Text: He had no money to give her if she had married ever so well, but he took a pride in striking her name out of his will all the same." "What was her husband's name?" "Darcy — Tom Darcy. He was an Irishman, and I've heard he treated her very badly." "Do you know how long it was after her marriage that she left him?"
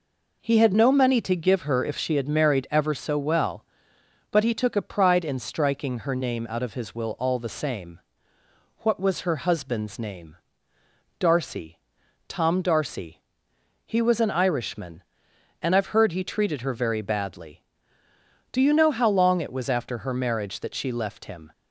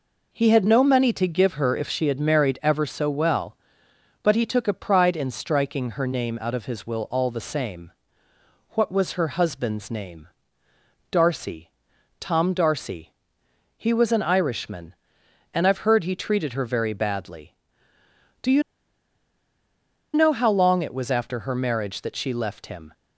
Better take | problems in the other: first | pauses between "you" and "know"; strong; at 18.6 s; 1.5 s long

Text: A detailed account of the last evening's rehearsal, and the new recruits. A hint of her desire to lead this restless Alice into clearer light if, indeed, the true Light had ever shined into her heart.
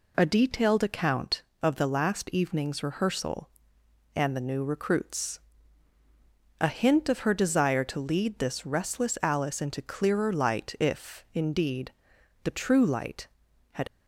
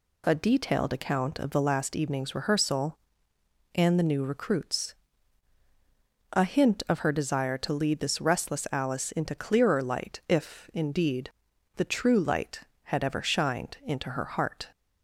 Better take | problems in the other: second | stops before "ever shined into her heart"; at 13.8 s

